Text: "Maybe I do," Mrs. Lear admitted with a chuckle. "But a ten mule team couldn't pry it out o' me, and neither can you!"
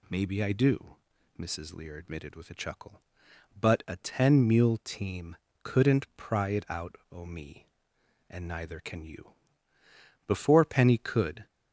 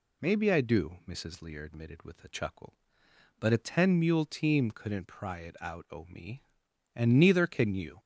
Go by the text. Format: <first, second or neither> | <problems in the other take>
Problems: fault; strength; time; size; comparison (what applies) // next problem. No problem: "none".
second | pauses between "team" and "couldn't"; slight; at 5.3 s; 0.24 s long // goes on to say "Before Penny could"; noticeable; from 10.2 s on; 1.2 s long